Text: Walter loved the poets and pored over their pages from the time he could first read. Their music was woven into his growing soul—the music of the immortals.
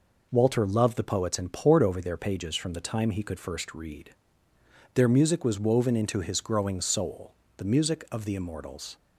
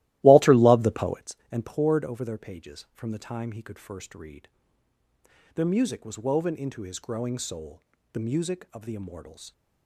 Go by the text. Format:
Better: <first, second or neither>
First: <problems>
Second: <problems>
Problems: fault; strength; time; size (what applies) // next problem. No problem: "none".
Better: first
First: none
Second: starts louder than the rest; strong; until 1.3 s; 16 dB